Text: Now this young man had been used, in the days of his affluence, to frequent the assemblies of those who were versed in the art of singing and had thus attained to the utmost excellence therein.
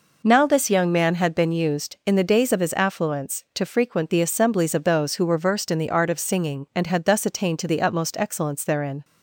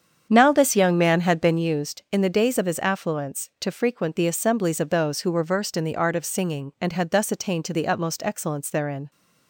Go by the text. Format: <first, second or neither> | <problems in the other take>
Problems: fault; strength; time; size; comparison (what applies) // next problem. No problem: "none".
first | starts louder than the rest; strong; until 1.7 s; 8 dB